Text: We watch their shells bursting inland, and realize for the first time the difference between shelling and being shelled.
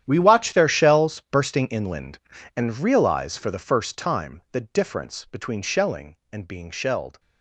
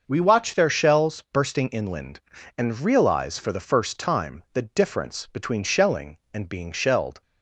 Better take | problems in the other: second | gets quieter; strong; throughout; 17 dB // starts louder than the rest; strong; until 1.0 s; 10.5 dB; also in the second

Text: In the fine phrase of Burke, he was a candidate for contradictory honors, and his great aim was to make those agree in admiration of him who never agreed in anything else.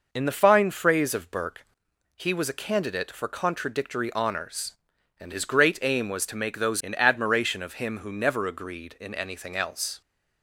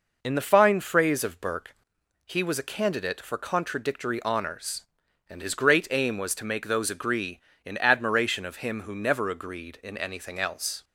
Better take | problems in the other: second | skips "agree"; at 6.8 s

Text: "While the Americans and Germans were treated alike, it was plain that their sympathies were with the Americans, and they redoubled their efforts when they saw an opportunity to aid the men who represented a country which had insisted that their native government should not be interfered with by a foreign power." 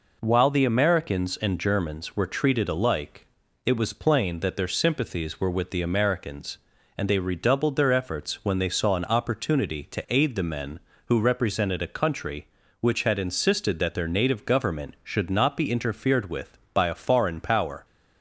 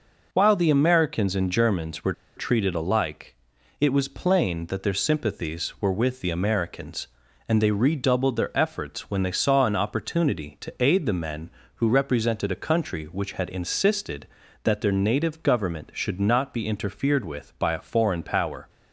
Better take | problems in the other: first | pauses between "were" and "treated"; slight; at 2.1 s; 0.23 s long

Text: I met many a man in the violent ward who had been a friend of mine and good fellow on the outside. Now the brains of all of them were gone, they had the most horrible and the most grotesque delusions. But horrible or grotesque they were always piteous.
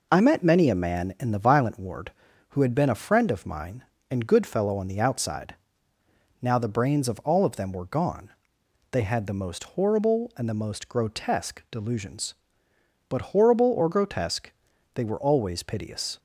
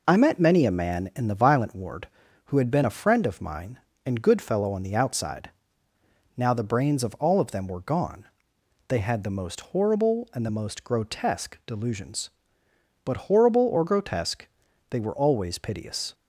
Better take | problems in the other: neither | pauses between "grotesque" and "they"; the same in both

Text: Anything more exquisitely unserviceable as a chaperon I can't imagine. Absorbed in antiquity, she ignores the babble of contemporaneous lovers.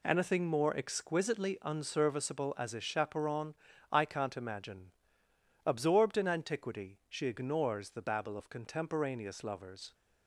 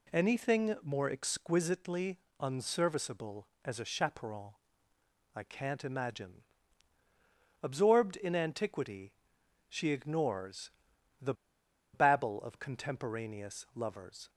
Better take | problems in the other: first | pauses between "exquisitely" and "unserviceable"; slight; at 2.1 s; 0.22 s long // pauses between "chaperon" and "I"; noticeable; at 4.5 s; 0.84 s long; also in the first // pauses between "ignores" and "the"; noticeable; at 10.6 s; 0.50 s long // pauses between "the" and "babble"; noticeable; at 11.3 s; 0.59 s long

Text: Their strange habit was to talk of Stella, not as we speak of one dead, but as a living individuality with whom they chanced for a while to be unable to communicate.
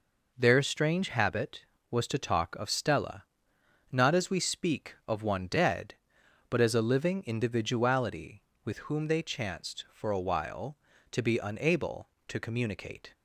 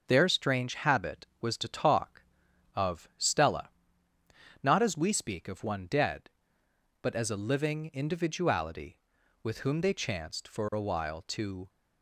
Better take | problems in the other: first | starts louder than the rest; until 1.0 s; 6.5 dB // stops before "be unable to communicate"; at 11.6 s

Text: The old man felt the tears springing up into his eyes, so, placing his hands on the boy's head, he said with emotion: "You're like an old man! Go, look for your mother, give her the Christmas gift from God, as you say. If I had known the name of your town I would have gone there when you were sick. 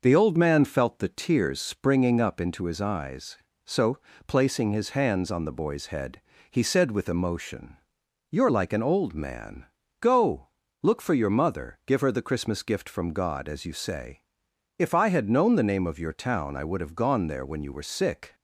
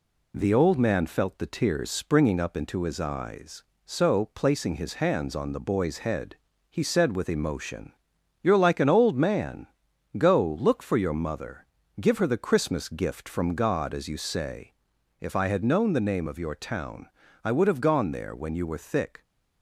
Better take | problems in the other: first | pauses between "town" and "I"; at 17.0 s; 0.38 s long // says "thick" for "sick"; at 18.7 s

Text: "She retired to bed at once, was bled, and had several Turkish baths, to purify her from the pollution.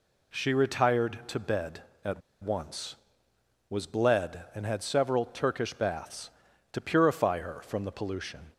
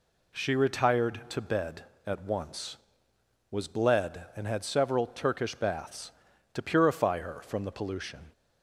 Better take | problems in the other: second | pauses between "at" and "once"; slight; at 2.2 s; 0.21 s long

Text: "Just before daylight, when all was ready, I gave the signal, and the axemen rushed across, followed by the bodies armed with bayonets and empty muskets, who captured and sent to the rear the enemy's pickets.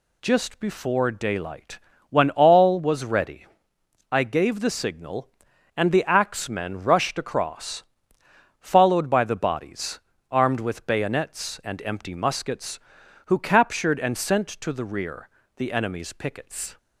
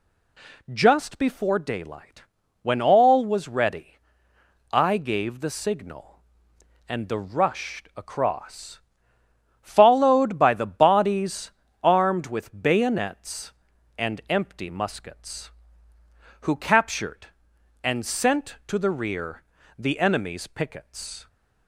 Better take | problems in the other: first | skips "axemen"; at 7.1 s // pauses between "bodies" and "armed"; slight; at 11.5 s; 0.32 s long; slight in the first // pauses between "rear" and "the"; slight; at 19.4 s; 0.36 s long; slight in the first

